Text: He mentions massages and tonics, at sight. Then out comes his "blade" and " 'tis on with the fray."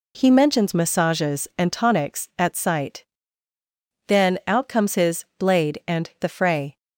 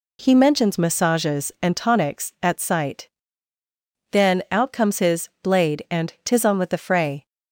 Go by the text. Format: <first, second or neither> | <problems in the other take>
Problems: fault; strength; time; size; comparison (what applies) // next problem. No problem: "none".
second | skips "tis on with"; at 6.2 s